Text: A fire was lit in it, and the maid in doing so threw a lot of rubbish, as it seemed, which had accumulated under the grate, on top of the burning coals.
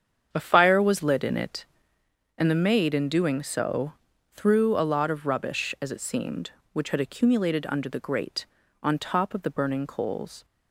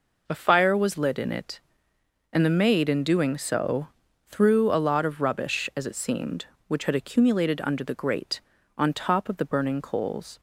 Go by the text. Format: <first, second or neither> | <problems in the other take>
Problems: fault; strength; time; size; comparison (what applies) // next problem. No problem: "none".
second | starts louder than the rest; strong; until 2.1 s; 7.5 dB // pauses between "so" and "threw"; at 3.9 s; 0.40 s long; also in the second